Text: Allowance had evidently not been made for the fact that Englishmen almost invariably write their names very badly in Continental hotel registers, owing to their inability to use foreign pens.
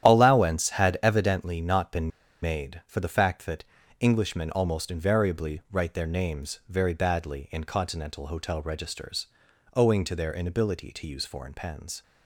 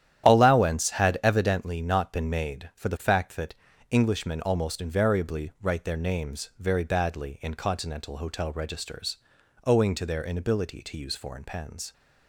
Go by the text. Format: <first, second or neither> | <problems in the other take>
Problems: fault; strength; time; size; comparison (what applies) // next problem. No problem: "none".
second | starts louder than the rest; strong; until 1.1 s; 10.5 dB; strong in the second // pauses between "been" and "made"; slight; at 2.1 s; 0.32 s long // pauses between "that" and "Englishmen"; at 3.6 s; 0.38 s long; also in the second